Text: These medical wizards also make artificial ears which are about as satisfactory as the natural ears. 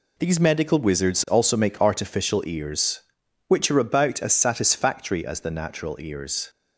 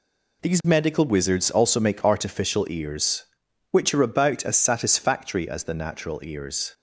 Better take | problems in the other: neither | none

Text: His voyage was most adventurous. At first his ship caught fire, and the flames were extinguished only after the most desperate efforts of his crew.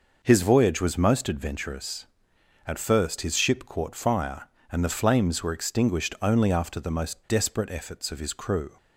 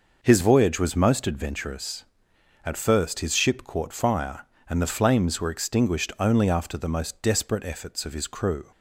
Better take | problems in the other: neither | none

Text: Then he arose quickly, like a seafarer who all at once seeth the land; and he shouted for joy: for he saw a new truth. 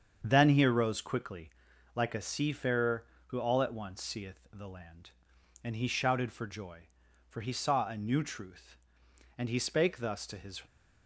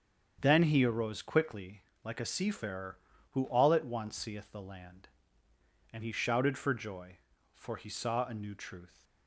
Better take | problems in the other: second | starts louder than the rest; strong; until 1.2 s; 7.5 dB; strong in the second // goes on to say "And he spake thus to his"; noticeable; from 9.3 s on; 1.2 s long

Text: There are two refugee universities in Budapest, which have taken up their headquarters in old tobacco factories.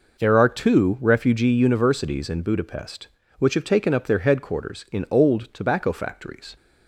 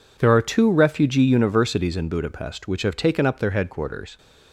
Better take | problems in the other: first | stops before "in old tobacco factories"; at 4.1 s

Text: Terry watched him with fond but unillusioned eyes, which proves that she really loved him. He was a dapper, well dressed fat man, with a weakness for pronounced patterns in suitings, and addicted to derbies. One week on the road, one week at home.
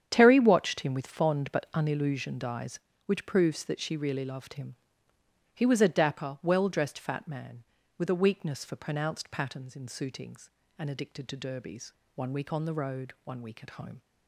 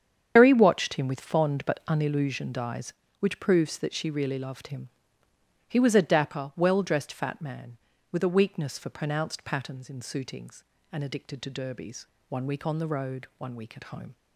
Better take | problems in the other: first | loses the start of "Terry"; at 0.3 s; 130 ms // starts louder than the rest; strong; until 1.3 s; 8 dB; strong in the first

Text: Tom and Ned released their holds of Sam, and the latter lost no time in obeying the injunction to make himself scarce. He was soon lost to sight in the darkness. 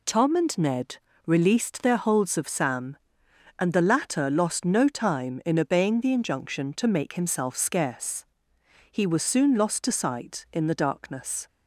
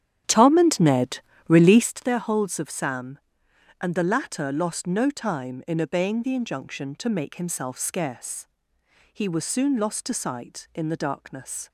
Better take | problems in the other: first | starts louder than the rest; strong; until 2.0 s; 10.5 dB // pauses between "Ned" and "released"; slight; at 1.1 s; 0.30 s long; slight in the first

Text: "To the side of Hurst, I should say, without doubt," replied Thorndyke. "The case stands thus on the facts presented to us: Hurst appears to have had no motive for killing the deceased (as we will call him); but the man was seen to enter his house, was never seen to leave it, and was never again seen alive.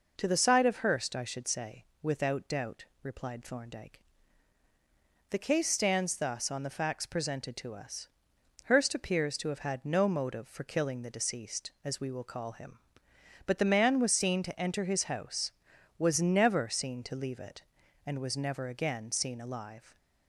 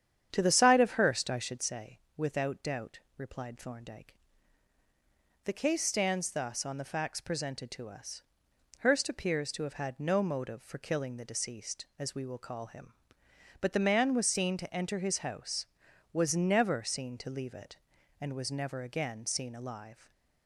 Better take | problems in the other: first | starts louder than the rest; strong; until 1.7 s; 9 dB

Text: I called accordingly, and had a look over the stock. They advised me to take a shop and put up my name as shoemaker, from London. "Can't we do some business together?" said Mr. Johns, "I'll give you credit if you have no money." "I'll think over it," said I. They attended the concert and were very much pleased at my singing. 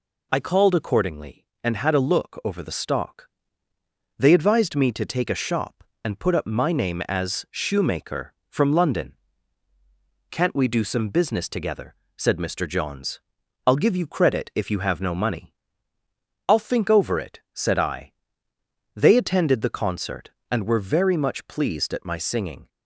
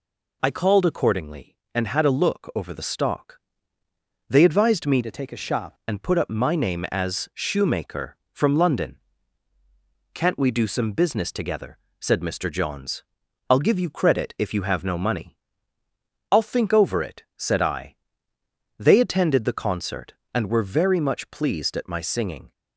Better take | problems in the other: first | changes voice from "to" to "shop"; from 5.0 to 5.7 s; 0.7 s long

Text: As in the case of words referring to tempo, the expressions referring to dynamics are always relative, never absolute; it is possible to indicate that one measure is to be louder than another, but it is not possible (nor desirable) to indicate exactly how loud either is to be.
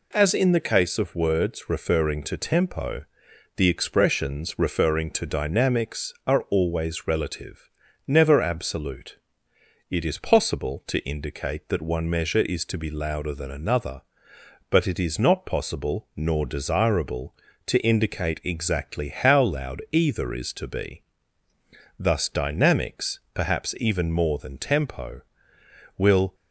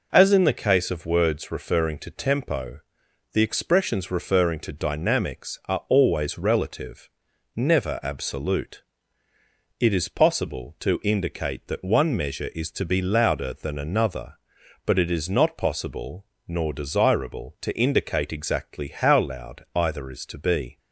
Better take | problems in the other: second | goes on to say "Thus dynamics perhaps even more than tempo will"; strong; from 21.9 s on; 4.3 s long

